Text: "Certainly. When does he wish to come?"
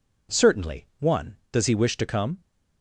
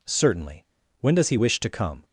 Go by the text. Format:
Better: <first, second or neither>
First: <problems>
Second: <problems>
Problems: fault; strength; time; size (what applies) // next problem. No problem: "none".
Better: second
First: says "One" for "When"; at 0.9 s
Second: none